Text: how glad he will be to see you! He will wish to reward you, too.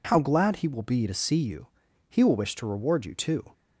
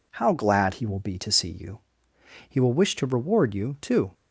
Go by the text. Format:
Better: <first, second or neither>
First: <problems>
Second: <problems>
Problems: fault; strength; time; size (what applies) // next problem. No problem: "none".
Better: neither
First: none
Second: none